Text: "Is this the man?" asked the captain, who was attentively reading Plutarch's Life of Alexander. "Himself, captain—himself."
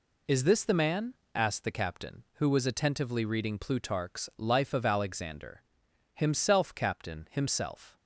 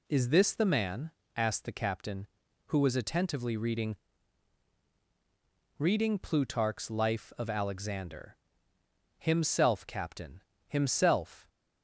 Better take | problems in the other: first | says "reading" twice; at 5.7 s

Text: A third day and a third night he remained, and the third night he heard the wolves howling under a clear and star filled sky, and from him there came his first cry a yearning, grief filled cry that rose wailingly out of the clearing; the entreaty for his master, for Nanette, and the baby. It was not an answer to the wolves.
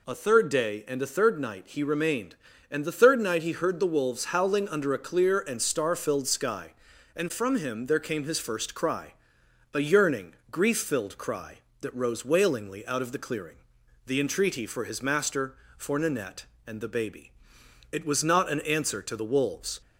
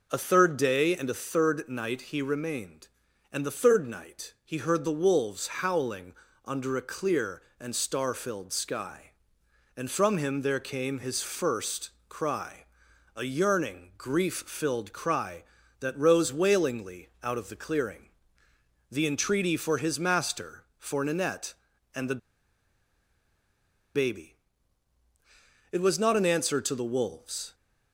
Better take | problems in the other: first | pauses between "howling" and "under"; slight; at 6.1 s; 0.32 s long // pauses between "first" and "cry"; slight; at 11.8 s; 0.18 s long // pauses between "cry" and "a"; noticeable; at 12.6 s; 0.56 s long; noticeable in the first // pauses between "wailingly" and "out"; slight; at 17.0 s; 0.16 s long // pauses between "the" and "baby"; strong; at 22.1 s; 1.7 s long

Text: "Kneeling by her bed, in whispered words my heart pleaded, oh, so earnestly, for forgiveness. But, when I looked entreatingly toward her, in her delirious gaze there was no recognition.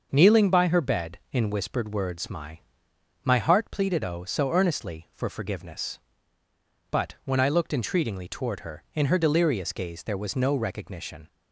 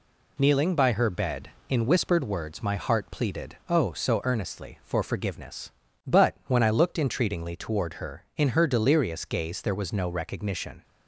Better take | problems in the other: second | starts louder than the rest; until 1.1 s; 6.5 dB // says "my" twice; at 3.2 s

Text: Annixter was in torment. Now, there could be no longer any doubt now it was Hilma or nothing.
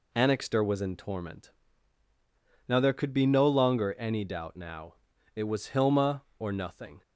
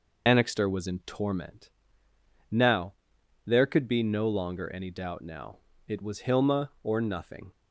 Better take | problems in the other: first | loses the start of "Annixter"; at 0.2 s; 65 ms // pauses between "now" and "it"; slight; at 5.5 s; 0.30 s long; also in the first

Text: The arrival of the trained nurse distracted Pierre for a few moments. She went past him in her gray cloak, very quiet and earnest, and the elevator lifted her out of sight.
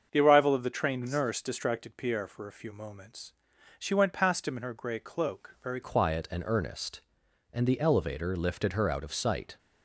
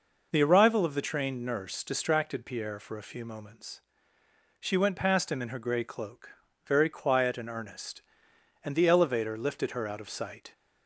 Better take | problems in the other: second | starts louder than the rest; until 1.1 s; 7 dB // changes voice at "quiet"; from 5.8 s on; 3.7 s long

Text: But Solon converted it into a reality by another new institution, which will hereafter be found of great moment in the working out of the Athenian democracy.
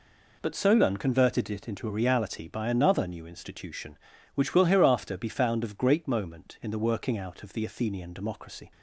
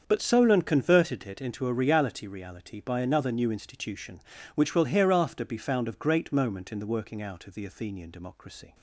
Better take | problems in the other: first | starts louder than the rest; until 1.0 s; 7 dB // says "reality" twice; at 2.2 s

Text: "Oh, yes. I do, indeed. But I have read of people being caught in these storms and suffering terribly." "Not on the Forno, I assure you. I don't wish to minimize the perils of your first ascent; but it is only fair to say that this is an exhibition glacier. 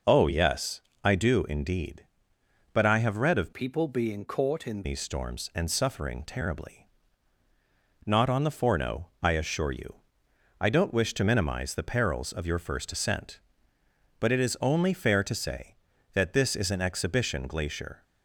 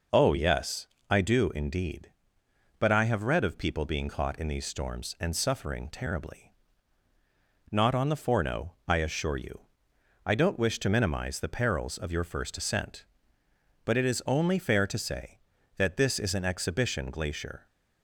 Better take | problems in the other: second | changes voice from "people" to "in"; from 3.5 to 4.8 s; 1.3 s long

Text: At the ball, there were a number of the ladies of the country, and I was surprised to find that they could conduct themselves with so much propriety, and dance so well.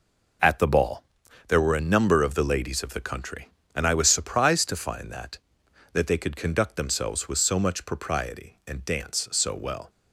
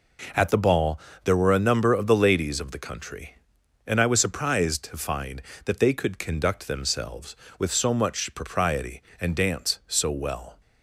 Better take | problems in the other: second | says "that" twice; at 5.9 s

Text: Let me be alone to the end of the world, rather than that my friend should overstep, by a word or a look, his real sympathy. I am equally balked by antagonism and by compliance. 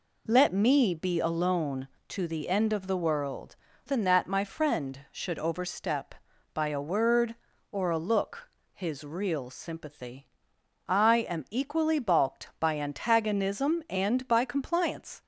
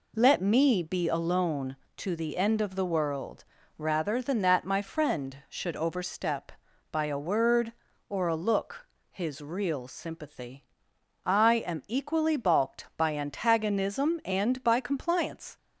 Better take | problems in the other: second | skips "rather"; at 3.7 s

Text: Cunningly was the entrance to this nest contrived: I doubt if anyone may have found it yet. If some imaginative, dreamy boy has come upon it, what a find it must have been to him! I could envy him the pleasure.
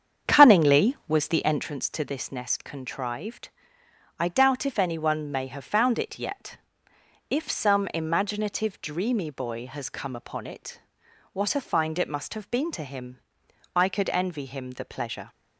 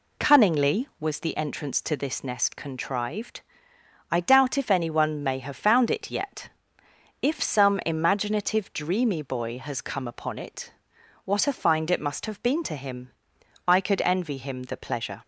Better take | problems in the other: second | starts louder than the rest; strong; until 1.7 s; 8 dB

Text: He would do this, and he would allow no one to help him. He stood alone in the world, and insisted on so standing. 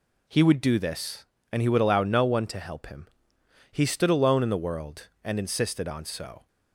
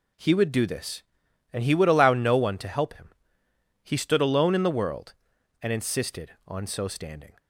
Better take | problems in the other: second | stops before "standing"; at 6.4 s

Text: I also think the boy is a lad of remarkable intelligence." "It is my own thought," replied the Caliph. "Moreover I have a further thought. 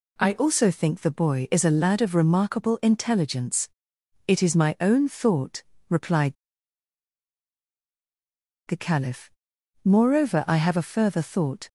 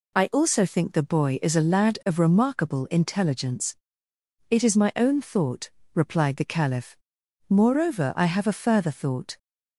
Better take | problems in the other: second | pauses between "replied" and "the"; strong; at 6.3 s; 2.3 s long

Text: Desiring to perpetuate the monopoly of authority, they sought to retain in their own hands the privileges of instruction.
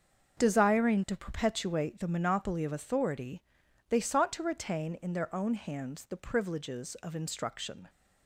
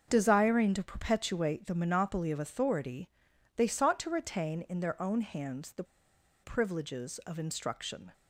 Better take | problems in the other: first | starts louder than the rest; until 1.0 s; 6.5 dB; also in the first // pauses between "the" and "privileges"; noticeable; at 5.8 s; 0.59 s long

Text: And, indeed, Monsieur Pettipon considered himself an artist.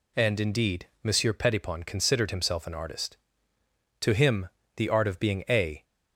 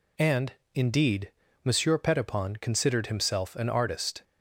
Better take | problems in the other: second | goes on to say "To him the art of being a"; strong; from 4.0 s on; 1.8 s long

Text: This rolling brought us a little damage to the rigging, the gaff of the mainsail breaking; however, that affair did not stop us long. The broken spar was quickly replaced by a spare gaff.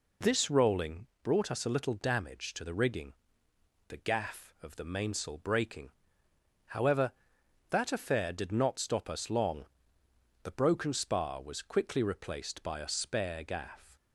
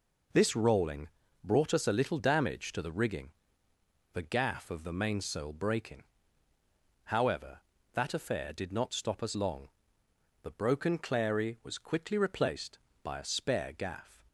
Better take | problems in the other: first | pauses between "rolling" and "brought"; slight; at 1.0 s; 0.34 s long; slight in the first // says "clary" for "spar"; at 10.9 s

